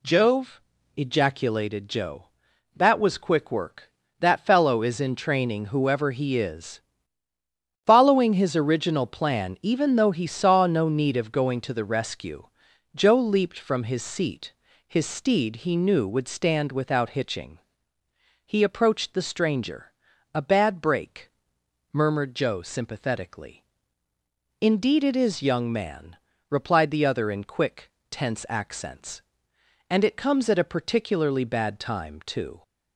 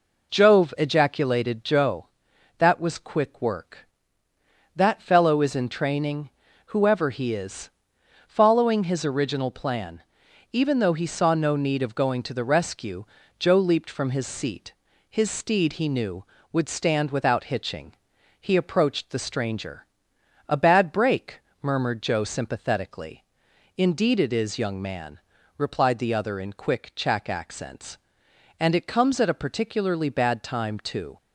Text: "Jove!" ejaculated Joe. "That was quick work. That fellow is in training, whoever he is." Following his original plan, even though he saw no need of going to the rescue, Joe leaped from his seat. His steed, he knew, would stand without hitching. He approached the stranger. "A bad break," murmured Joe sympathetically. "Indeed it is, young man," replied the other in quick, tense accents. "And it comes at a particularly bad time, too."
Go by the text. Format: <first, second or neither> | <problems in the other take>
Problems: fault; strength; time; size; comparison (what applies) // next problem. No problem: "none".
first | says "chack" for "tense"; at 26.9 s